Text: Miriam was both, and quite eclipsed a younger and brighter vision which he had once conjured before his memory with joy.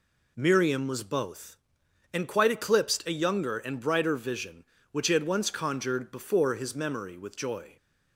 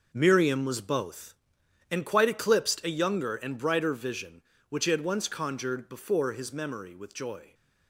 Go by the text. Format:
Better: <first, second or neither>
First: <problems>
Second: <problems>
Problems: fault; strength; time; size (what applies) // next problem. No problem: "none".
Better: first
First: none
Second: gets quieter; strong; throughout; 10.5 dB